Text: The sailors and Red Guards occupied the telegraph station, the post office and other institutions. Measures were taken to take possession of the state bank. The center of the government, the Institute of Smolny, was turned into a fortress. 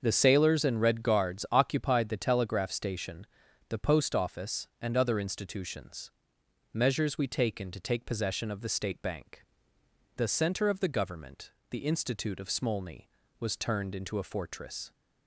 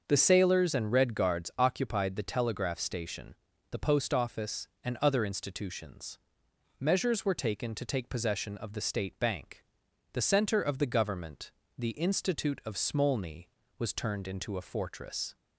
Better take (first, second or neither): second